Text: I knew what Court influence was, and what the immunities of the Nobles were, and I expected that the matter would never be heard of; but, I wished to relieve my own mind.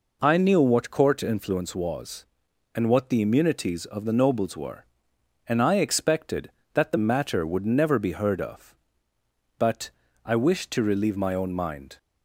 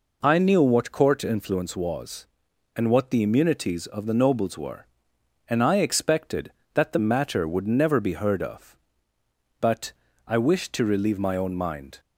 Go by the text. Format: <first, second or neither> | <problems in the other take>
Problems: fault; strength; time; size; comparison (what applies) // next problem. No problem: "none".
neither | none